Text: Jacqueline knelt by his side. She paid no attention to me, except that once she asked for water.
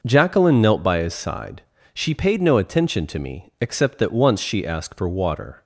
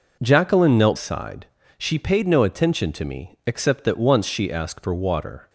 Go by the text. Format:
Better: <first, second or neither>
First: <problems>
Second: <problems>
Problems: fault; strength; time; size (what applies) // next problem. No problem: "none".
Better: first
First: none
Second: skips "by his"; at 0.9 s